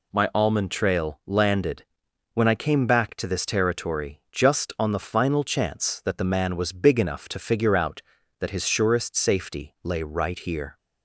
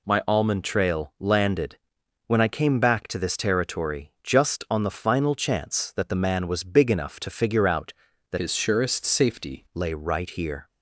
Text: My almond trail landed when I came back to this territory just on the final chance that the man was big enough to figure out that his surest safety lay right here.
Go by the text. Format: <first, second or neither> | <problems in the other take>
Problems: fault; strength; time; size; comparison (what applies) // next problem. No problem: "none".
first | pauses between "landed" and "when"; noticeable; at 1.7 s; 0.50 s long; noticeable in the first // changes voice from "his" to "safety"; from 8.3 to 9.6 s; 1.3 s long